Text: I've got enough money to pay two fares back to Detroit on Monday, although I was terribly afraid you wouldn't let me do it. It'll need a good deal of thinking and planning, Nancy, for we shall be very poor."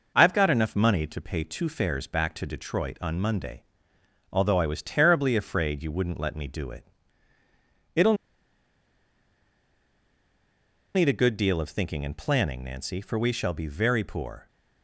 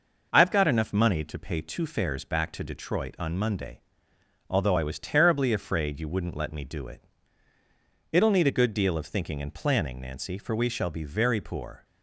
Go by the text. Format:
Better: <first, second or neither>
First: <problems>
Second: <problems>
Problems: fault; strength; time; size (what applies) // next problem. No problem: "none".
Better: second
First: pauses between "It'll" and "need"; strong; at 8.1 s; 2.8 s long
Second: none